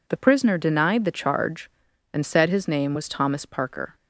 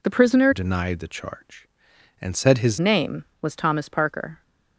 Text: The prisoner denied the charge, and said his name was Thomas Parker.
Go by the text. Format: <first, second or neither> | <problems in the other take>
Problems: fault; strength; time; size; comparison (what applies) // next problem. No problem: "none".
first | changes voice from "denied" to "his"; from 0.5 to 2.7 s; 2.2 s long